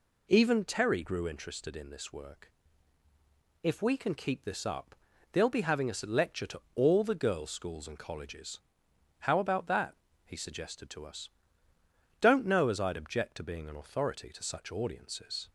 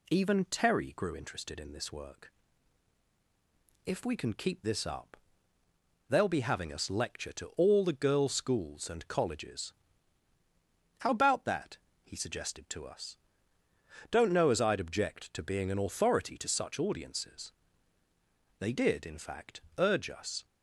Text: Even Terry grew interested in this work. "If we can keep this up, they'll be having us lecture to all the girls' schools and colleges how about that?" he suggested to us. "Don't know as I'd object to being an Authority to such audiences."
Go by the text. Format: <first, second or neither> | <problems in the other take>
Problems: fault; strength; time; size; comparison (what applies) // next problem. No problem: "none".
first | pauses between "colleges" and "how"; strong; at 9.7 s; 1.2 s long; noticeable in the first // goes on to say "They did in fact urge us"; strong; from 18.5 s on; 1.8 s long